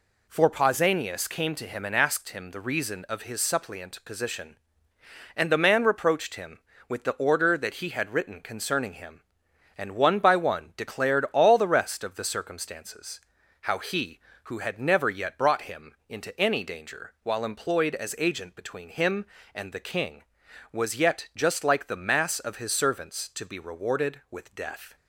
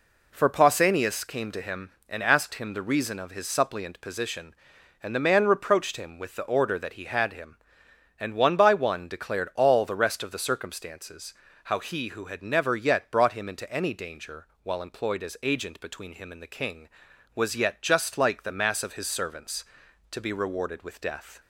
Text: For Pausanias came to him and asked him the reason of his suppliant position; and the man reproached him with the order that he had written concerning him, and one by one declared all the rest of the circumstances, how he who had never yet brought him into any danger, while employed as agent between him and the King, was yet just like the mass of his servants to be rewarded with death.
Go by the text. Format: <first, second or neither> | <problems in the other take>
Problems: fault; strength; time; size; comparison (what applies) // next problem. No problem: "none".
first | skips "written concerning"; at 7.3 s